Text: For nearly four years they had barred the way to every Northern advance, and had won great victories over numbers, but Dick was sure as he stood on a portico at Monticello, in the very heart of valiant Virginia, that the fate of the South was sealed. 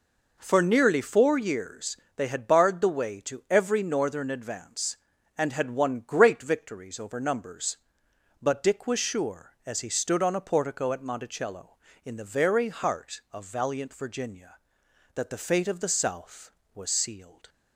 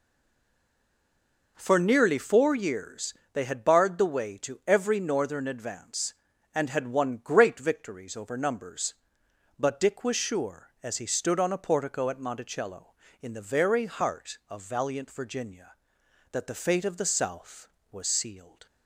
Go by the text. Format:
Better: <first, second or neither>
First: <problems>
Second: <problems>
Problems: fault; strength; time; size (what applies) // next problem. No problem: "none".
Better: first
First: pauses between "years" and "they"; slight; at 1.9 s; 0.18 s long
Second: stays silent before the first word; noticeable; until 1.5 s; 1.5 s long // pauses between "years" and "they"; slight; at 3.1 s; 0.18 s long